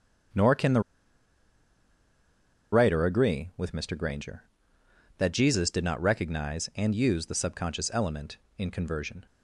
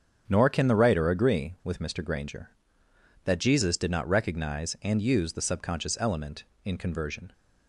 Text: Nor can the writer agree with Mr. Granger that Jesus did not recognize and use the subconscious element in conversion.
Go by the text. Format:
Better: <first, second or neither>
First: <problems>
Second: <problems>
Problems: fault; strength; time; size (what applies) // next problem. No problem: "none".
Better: second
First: starts louder than the rest; strong; until 3.2 s; 8 dB // pauses between "the" and "writer"; strong; at 0.7 s; 1.9 s long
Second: starts louder than the rest; strong; until 1.2 s; 7.5 dB